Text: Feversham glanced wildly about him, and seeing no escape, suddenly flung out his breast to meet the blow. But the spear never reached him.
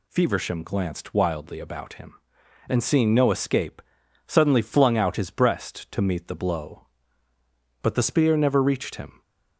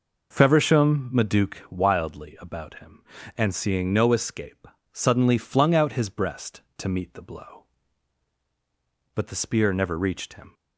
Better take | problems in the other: first | says "maduke" for "glanced"; at 1.1 s

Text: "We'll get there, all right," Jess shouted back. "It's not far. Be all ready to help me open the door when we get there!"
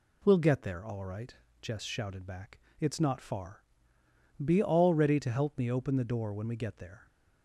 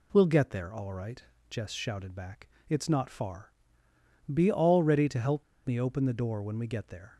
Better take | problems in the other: first | pauses between "help" and "me"; slight; at 5.4 s; 0.23 s long

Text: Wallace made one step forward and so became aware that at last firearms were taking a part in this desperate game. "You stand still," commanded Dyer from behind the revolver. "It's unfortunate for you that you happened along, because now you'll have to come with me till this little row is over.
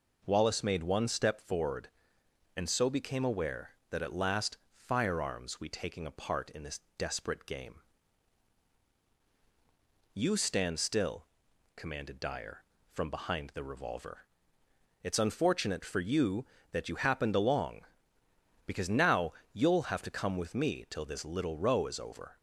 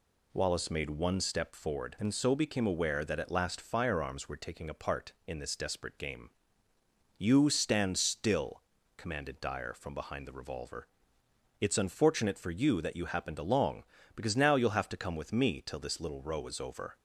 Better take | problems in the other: second | says "we" for "were"; at 5.5 s // pauses between "this" and "desperate"; slight; at 6.7 s; 0.20 s long // pauses between "now" and "you'll"; slight; at 19.3 s; 0.22 s long

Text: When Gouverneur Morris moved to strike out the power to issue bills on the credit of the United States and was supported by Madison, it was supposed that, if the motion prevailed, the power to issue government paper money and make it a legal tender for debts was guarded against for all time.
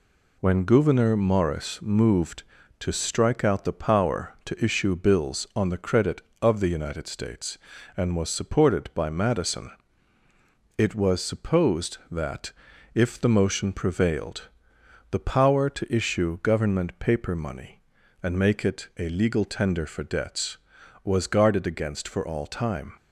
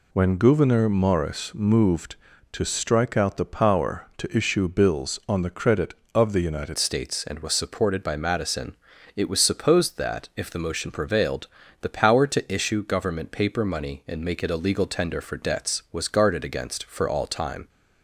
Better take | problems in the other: first | changes voice at "States"; from 6.7 s on; 10.9 s long

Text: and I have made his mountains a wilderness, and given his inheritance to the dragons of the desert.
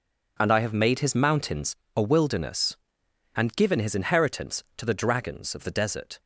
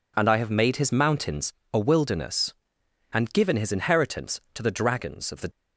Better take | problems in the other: first | pauses between "mountains" and "a"; slight; at 1.5 s; 0.20 s long; slight in the first // stops before "desert"; at 5.5 s

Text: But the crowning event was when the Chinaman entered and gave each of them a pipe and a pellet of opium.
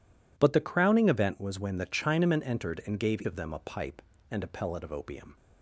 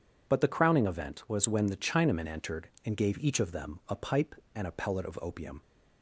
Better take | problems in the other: second | skips "each"; at 3.2 s

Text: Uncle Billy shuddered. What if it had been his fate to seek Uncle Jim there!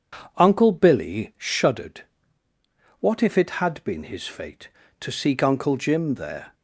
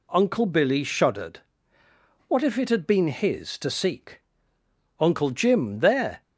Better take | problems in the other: first | skips "fate"; at 3.5 s // pauses between "seek" and "Uncle"; noticeable; at 4.2 s; 0.80 s long

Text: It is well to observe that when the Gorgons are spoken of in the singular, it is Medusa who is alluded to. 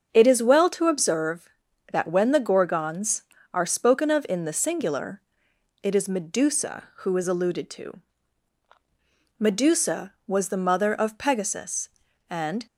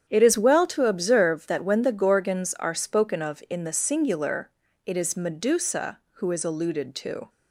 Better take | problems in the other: second | starts louder than the rest; strong; until 1.1 s; 7 dB; strong in the second // goes on to say "Medusa was the mother of Pegasus and"; strong; from 9.3 s on; 3.2 s long

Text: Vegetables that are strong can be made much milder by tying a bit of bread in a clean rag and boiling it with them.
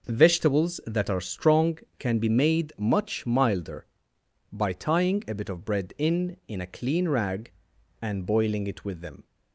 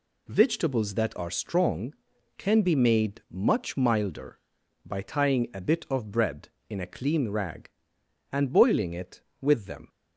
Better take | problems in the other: second | says "in" twice; at 6.4 s

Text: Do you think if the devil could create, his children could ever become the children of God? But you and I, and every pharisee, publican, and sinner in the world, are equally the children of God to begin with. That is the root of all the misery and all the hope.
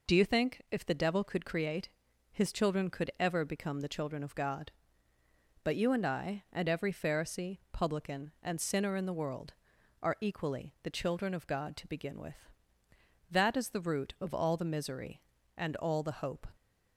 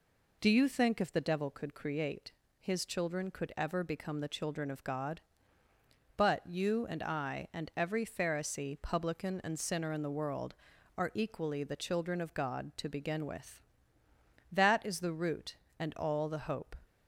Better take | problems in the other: first | skips "of all the misery"; at 15.6 s

